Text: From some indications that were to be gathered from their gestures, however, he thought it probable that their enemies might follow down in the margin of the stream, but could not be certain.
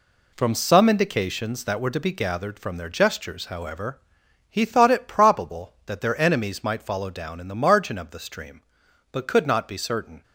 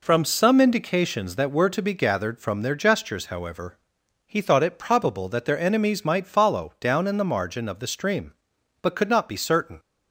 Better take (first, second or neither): second